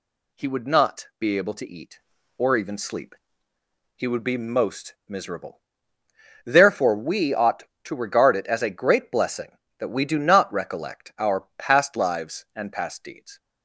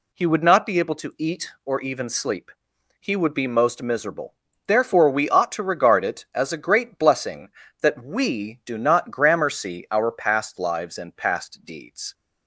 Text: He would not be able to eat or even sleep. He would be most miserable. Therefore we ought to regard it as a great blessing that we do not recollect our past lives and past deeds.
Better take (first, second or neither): first